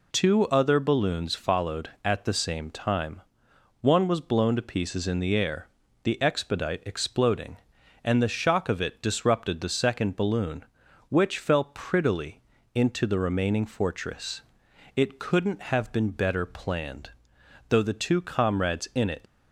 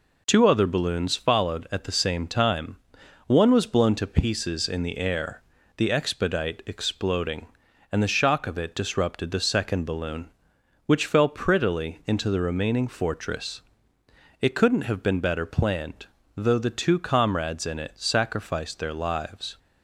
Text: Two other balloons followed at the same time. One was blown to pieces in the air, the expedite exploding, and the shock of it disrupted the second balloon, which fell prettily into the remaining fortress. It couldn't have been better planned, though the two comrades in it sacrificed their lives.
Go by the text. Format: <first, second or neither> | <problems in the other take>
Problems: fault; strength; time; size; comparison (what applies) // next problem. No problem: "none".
second | pauses between "prettily" and "into"; slight; at 12.4 s; 0.34 s long // stops before "sacrificed their lives"; at 19.2 s